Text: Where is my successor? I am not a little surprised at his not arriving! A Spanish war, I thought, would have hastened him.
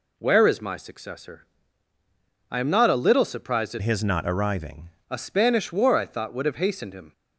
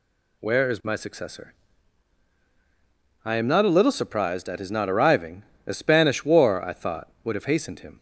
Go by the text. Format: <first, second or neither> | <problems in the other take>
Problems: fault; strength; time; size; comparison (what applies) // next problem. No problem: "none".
second | changes voice from "his" to "arriving"; from 3.8 to 4.9 s; 1.1 s long